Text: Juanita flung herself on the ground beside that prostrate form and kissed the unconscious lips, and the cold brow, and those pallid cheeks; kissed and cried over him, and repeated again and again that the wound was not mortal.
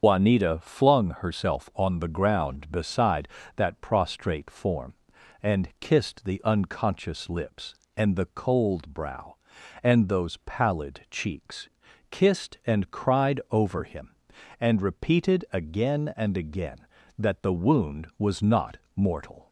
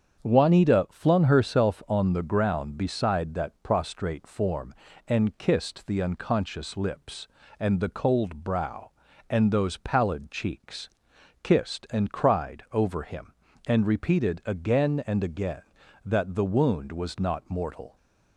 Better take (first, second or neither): second